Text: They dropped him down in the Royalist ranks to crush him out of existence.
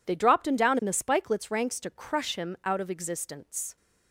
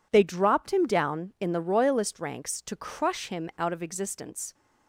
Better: second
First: says "Spikelets" for "Royalist"; at 0.9 s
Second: none

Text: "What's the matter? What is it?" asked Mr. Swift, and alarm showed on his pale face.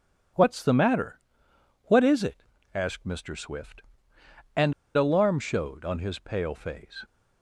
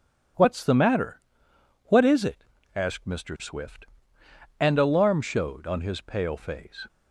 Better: second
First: pauses between "and" and "alarm"; slight; at 4.7 s; 0.23 s long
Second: none

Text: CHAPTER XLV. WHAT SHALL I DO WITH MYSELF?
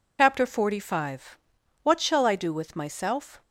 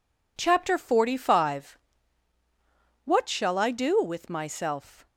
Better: second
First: loses the start of "CHAPTER"; at 0.1 s; 70 ms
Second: none

